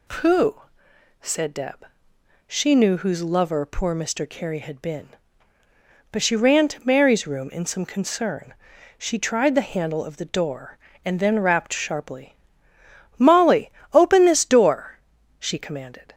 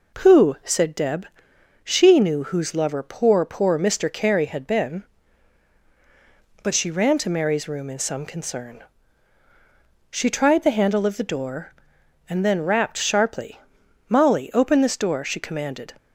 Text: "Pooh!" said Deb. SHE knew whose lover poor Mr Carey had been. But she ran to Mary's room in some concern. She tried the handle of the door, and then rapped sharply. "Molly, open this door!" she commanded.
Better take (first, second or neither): first